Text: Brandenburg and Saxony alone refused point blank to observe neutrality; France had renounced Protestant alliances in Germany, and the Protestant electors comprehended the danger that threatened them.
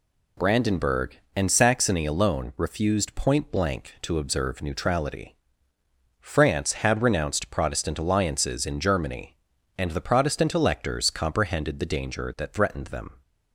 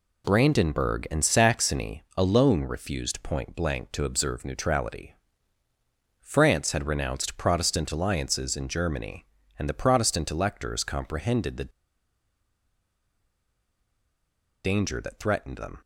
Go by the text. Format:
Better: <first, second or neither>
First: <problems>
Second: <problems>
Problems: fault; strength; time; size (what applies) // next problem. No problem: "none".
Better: first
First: none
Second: pauses between "Saxony" and "alone"; slight; at 2.0 s; 0.16 s long // pauses between "the" and "danger"; strong; at 11.7 s; 2.9 s long